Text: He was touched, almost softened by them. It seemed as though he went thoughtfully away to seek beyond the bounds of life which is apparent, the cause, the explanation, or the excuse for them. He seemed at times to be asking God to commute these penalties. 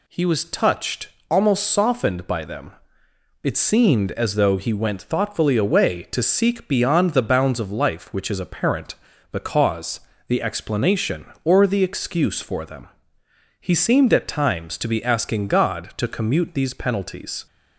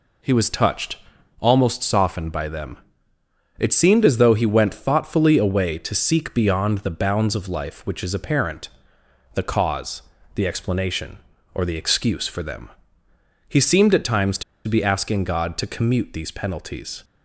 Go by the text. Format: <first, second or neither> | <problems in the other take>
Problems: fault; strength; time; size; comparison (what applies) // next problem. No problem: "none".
first | pauses between "to" and "be"; slight; at 14.4 s; 0.24 s long